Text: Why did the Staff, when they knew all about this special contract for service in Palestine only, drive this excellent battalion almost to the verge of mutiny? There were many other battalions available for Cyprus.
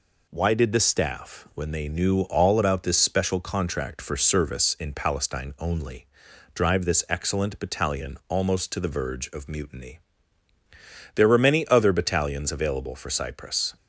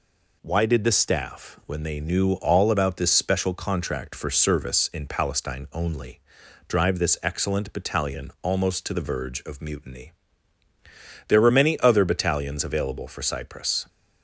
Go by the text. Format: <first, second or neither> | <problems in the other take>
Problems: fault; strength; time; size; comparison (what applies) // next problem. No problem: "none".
neither | none